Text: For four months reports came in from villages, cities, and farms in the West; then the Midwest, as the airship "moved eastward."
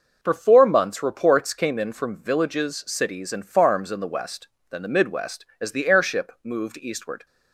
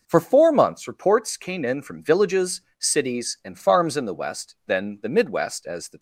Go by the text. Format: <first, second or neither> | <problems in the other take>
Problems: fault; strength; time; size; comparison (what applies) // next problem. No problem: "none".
first | stops before "airship moved eastward"; at 5.9 s